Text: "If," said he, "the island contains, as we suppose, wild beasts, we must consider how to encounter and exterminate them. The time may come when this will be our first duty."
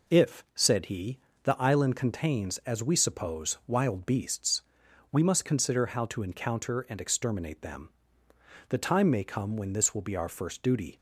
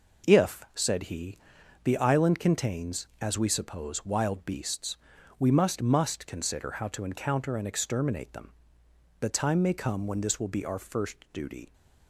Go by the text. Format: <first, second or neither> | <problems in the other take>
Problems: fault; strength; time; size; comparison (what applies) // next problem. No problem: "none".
first | says "must" twice; at 5.8 s